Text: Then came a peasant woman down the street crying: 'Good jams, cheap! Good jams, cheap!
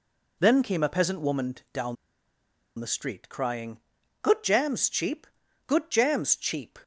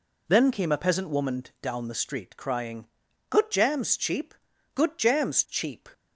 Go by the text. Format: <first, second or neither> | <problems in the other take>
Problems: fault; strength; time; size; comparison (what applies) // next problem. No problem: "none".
second | pauses between "woman" and "down"; slight; at 1.5 s; 0.18 s long; slight in the second // pauses between "down" and "the"; noticeable; at 1.9 s; 0.83 s long